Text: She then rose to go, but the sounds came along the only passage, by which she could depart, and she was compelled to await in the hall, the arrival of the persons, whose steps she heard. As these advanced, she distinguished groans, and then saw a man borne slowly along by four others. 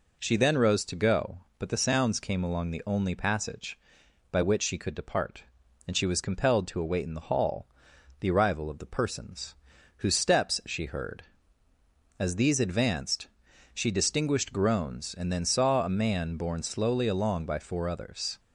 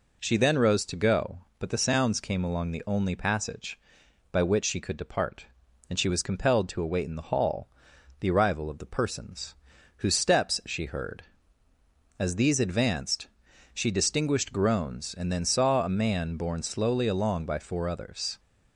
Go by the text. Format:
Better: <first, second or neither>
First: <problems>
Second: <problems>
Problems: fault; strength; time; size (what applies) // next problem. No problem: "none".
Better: neither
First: none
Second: none